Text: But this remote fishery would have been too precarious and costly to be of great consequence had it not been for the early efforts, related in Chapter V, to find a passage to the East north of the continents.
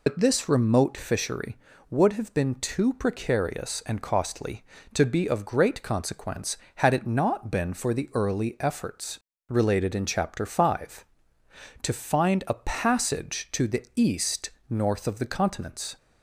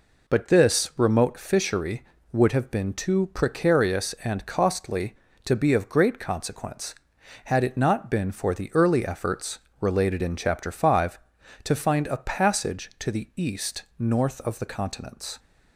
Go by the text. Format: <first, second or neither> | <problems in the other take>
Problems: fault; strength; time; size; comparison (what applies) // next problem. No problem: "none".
second | loses the start of "But"; at 0.0 s; 75 ms // pauses between "East" and "north"; slight; at 14.4 s; 0.20 s long; slight in the second